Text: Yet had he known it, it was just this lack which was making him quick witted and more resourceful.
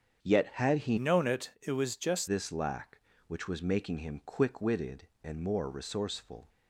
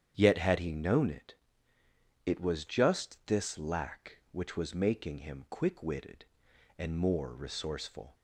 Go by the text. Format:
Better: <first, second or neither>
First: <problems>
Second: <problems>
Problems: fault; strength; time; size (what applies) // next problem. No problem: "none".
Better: second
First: starts louder than the rest; strong; until 1.3 s; 8 dB // changes voice from "known" to "just"; from 0.9 to 2.2 s; 1.3 s long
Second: starts louder than the rest; strong; until 1.1 s; 8.5 dB